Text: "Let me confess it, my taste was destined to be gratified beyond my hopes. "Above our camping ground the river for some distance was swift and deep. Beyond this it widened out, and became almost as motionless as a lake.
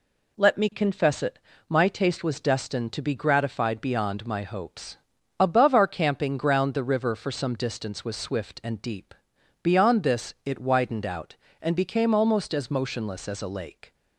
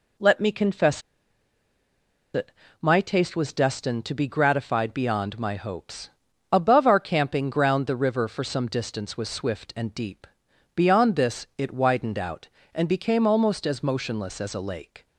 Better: first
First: none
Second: pauses between "confess" and "it"; strong; at 1.0 s; 1.3 s long

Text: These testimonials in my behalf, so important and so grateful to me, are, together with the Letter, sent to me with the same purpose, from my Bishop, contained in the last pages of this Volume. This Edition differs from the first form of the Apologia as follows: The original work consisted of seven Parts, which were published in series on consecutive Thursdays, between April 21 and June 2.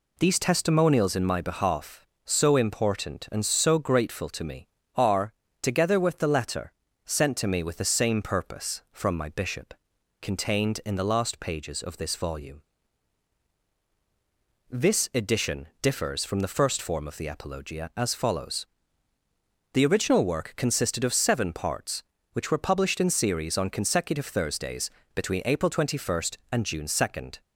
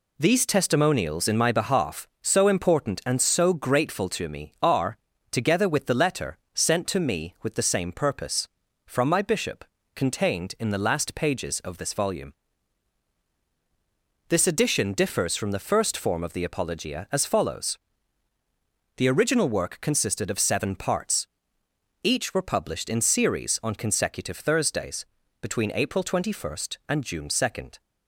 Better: first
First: none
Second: says "each" for "which"; at 22.0 s

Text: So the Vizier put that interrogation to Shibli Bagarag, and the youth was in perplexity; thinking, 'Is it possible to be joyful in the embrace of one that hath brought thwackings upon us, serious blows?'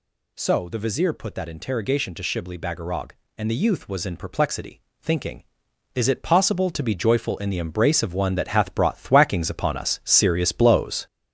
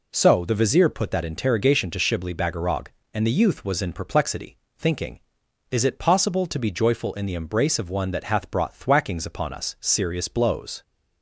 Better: second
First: gets louder; noticeable; throughout; 6 dB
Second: none

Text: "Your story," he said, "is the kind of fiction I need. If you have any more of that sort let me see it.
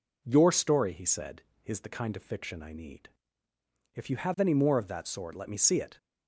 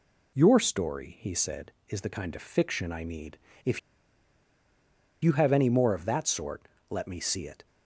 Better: first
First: none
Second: pauses between "If" and "you"; strong; at 3.7 s; 1.4 s long // pauses between "sort" and "let"; slight; at 6.6 s; 0.20 s long

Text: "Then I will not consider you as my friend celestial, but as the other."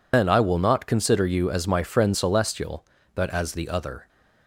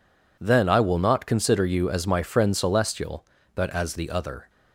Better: second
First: loses the start of "Then"; at 0.1 s; 135 ms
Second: none

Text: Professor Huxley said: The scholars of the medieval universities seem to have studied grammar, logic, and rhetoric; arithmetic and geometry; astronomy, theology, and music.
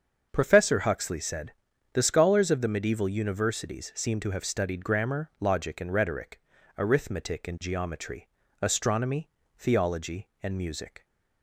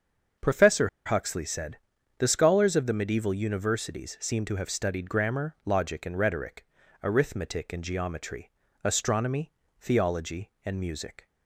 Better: first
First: starts louder than the rest; until 1.3 s; 6.5 dB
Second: starts louder than the rest; until 1.5 s; 6.5 dB // pauses between "Professor" and "Huxley"; slight; at 0.8 s; 0.17 s long

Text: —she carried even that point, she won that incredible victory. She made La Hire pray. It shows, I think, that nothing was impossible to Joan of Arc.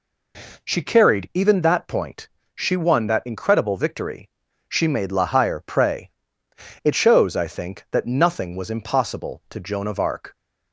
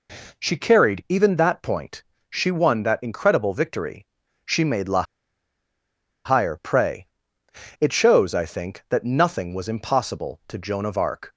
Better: first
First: none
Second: pauses between "La" and "Hire"; at 5.0 s; 1.2 s long

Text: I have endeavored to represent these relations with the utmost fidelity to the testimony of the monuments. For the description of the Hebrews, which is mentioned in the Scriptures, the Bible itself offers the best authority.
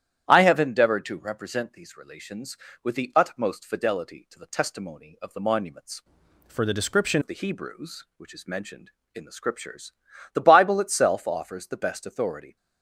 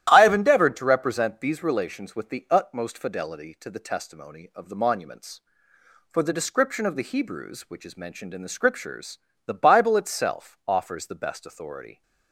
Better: second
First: starts louder than the rest; strong; until 1.3 s; 11 dB // changes voice from "For" to "description"; from 6.4 to 7.2 s; 0.8 s long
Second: starts louder than the rest; strong; until 1.1 s; 12.5 dB

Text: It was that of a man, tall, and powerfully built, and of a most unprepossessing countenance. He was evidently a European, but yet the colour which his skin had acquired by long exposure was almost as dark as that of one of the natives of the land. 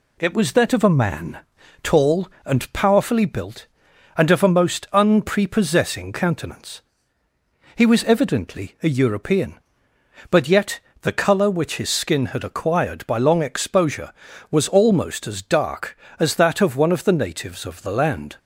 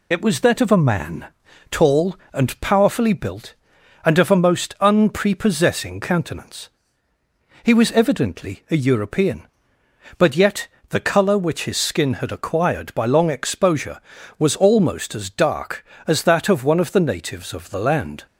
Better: first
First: pauses between "yet" and "the"; slight; at 10.7 s; 0.22 s long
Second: loses the start of "It"; at 0.1 s; 30 ms // pauses between "yet" and "the"; slight; at 10.6 s; 0.22 s long

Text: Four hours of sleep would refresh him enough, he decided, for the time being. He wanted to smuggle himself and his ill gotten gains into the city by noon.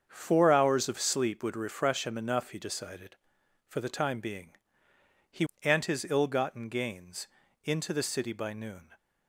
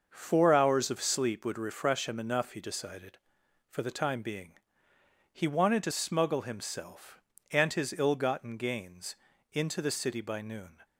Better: second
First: starts louder than the rest; strong; until 1.0 s; 7 dB // skips "wanted to smuggle himself"; at 5.5 s // pauses between "gains" and "into"; slight; at 7.2 s; 0.36 s long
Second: starts louder than the rest; noticeable; until 1.1 s; 6 dB // pauses between "gains" and "into"; slight; at 9.1 s; 0.36 s long

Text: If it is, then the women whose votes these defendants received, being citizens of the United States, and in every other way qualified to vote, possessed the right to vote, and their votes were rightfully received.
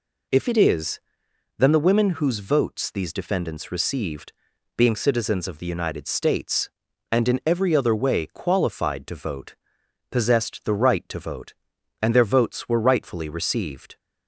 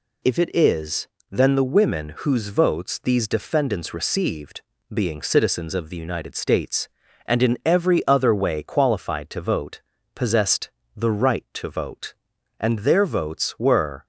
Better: first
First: none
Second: pauses between "possessed" and "the"; slight; at 10.6 s; 0.26 s long // stops before "rightfully received"; at 14.0 s

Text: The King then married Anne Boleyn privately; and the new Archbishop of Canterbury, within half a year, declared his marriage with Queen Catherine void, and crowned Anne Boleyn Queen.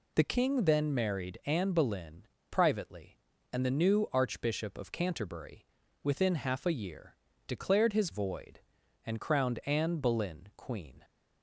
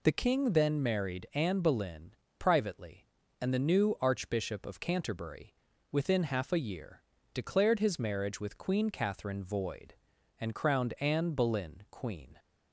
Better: second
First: pauses between "Boleyn" and "privately"; slight; at 2.2 s; 0.24 s long // skips "marriage with Queen Catherine"; at 8.1 s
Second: pauses between "Boleyn" and "privately"; slight; at 2.1 s; 0.24 s long

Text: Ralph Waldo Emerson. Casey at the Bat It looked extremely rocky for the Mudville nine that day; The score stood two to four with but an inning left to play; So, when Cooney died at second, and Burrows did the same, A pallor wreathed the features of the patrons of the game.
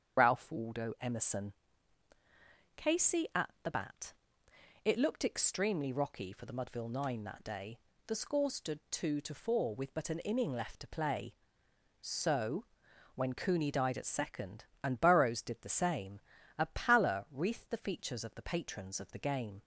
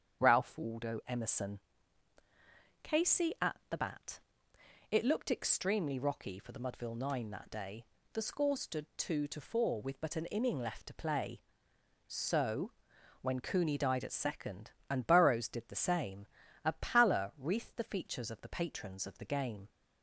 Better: second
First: loses the start of "Ralph"; at 0.1 s; 35 ms // starts louder than the rest; strong; until 1.2 s; 7.5 dB // pauses between "Bat" and "It"; noticeable; at 4.1 s; 0.72 s long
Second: starts louder than the rest; strong; until 1.2 s; 7.5 dB // pauses between "Bat" and "It"; noticeable; at 4.1 s; 0.72 s long

